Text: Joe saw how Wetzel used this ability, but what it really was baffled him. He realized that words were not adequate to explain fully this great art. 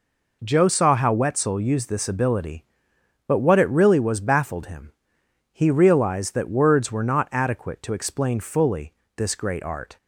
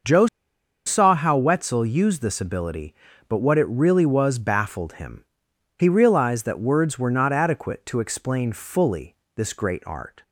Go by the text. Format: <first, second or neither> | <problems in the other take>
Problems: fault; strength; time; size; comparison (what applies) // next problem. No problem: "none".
first | starts louder than the rest; until 1.6 s; 6.5 dB // pauses between "Joe" and "saw"; noticeable; at 0.2 s; 0.59 s long // pauses between "fully" and "this"; slight; at 9.1 s; 0.20 s long; slight in the first